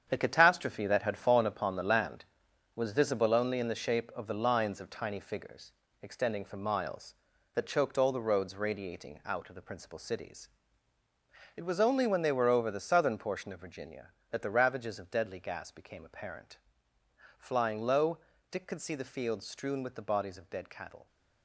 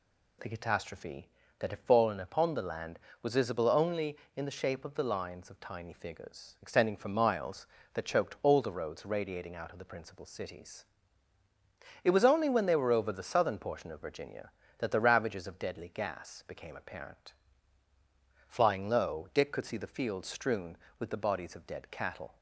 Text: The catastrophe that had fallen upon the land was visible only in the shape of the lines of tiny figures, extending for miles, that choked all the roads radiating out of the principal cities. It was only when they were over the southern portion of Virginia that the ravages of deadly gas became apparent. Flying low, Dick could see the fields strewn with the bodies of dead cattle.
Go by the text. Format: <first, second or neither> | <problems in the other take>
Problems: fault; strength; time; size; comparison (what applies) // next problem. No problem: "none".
second | gets quieter; strong; throughout; 9 dB